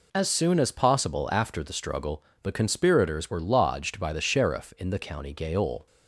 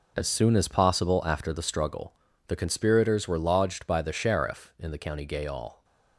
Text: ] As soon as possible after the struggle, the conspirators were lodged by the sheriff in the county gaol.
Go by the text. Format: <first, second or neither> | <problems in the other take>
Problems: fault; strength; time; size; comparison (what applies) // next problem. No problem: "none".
first | gets quieter; strong; throughout; 10.5 dB